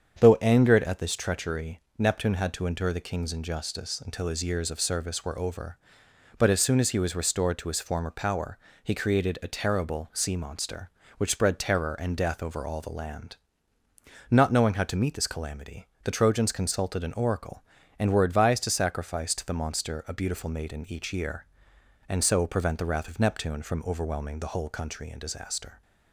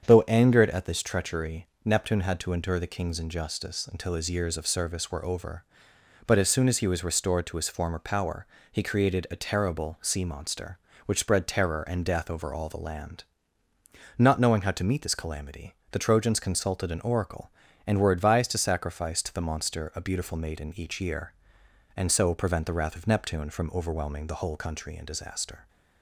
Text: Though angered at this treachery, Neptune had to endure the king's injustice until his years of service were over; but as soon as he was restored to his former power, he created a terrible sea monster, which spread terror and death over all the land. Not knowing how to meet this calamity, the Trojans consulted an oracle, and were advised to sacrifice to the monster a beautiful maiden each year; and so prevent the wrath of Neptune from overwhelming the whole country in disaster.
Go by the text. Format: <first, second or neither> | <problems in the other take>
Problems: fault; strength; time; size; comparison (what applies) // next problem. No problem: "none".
neither | starts louder than the rest; strong; the same in both